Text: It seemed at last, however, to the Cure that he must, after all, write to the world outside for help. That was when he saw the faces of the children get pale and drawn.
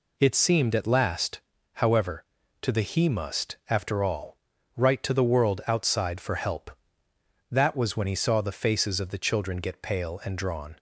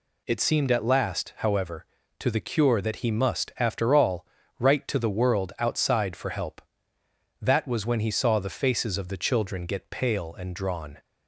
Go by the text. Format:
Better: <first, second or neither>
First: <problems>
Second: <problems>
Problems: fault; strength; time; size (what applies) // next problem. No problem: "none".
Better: second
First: skips "Cure that"; at 2.8 s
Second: none